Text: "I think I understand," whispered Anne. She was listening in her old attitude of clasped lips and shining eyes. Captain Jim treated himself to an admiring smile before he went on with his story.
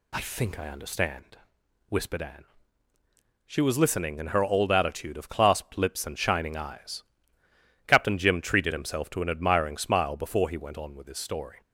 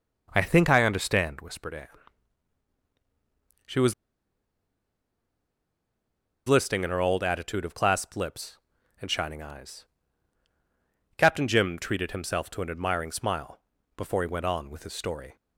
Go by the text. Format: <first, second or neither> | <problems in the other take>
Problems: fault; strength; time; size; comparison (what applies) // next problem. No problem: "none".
first | pauses between "was" and "listening"; strong; at 3.9 s; 2.5 s long // pauses between "smile" and "before"; slight; at 13.5 s; 0.36 s long